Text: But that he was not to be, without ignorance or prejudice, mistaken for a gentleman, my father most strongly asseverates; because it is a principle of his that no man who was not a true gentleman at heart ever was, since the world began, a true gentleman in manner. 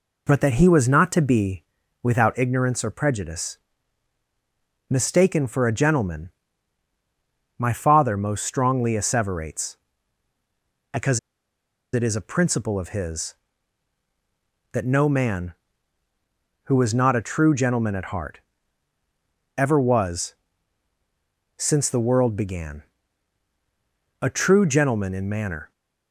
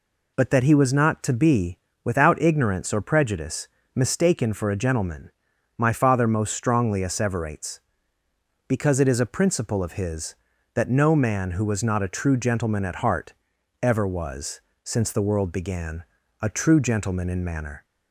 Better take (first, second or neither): second